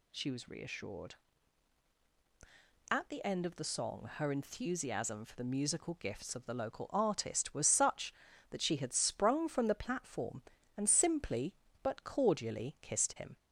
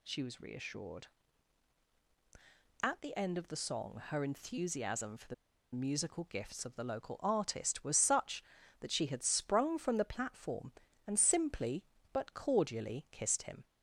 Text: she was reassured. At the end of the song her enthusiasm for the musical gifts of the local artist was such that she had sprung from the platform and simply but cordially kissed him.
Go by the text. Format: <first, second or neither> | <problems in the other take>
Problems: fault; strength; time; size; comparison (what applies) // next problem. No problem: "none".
first | pauses between "the" and "musical"; at 5.3 s; 0.39 s long